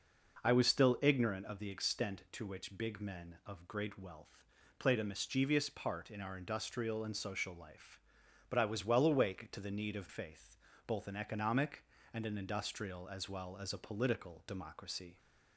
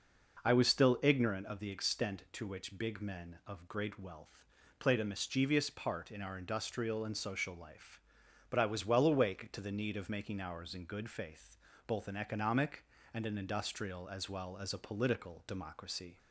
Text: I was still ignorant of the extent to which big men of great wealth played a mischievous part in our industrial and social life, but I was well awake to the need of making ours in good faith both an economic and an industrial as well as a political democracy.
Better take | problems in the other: second | pauses between "wealth" and "played"; slight; at 4.4 s; 0.34 s long; slight in the second // skips "making ours in good"; at 10.0 s // pauses between "faith" and "both"; slight; at 10.5 s; 0.32 s long; slight in the second

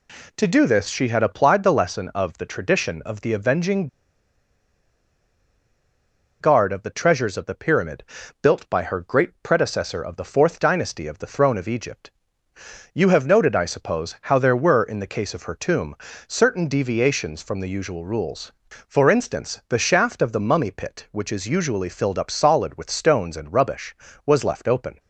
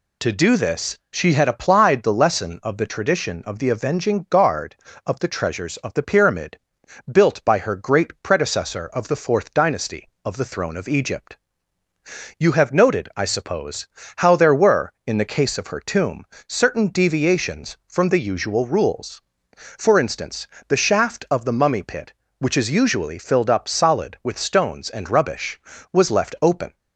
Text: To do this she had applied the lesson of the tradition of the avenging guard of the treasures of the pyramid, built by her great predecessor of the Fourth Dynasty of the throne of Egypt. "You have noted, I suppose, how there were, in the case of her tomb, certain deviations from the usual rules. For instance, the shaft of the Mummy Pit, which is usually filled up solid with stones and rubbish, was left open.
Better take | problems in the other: second | pauses between "avenging" and "guard"; strong; at 3.8 s; 2.5 s long

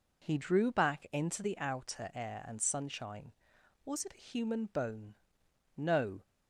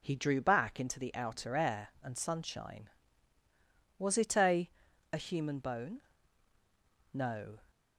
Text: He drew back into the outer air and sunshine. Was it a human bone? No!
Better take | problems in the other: first | says "a" twice; at 5.1 s

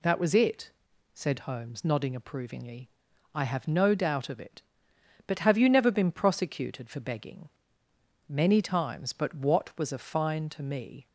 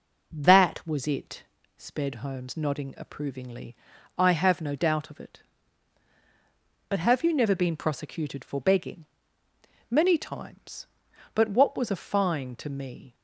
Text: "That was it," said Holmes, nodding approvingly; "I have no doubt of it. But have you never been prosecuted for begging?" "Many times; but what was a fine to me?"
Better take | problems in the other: first | says "sped" for "said"; at 1.7 s

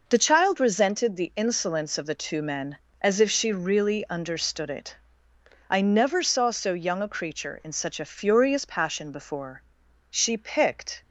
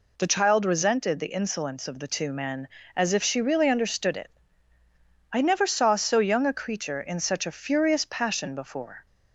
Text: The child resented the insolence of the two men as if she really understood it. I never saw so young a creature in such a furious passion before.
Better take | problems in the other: second | goes on to say "She picked"; noticeable; from 10.1 s on; 0.90 s long

